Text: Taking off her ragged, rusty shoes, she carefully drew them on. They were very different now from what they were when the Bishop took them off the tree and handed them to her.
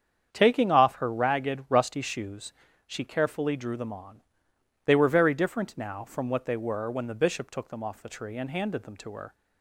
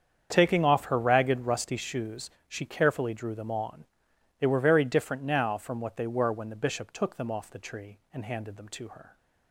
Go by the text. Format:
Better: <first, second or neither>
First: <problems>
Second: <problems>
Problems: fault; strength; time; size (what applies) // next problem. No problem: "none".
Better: neither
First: starts louder than the rest; strong; until 1.3 s; 8 dB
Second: starts louder than the rest; strong; until 1.3 s; 7.5 dB